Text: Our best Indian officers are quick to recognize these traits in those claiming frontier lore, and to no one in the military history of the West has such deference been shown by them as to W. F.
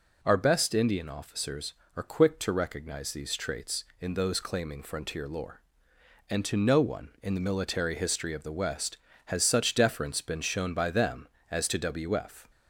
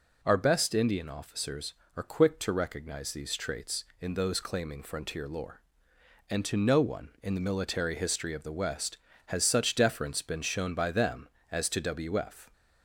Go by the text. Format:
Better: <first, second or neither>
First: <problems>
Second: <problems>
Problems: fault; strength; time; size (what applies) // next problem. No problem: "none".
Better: neither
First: none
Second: none